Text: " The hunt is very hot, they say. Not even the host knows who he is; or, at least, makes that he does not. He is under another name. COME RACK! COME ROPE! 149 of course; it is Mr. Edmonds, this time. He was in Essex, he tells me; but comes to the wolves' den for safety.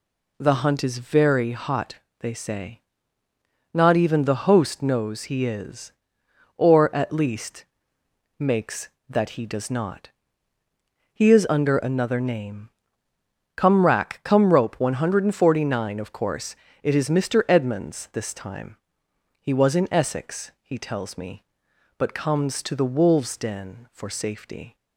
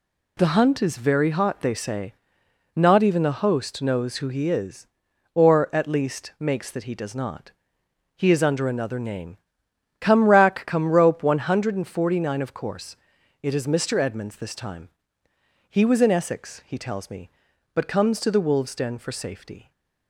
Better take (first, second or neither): second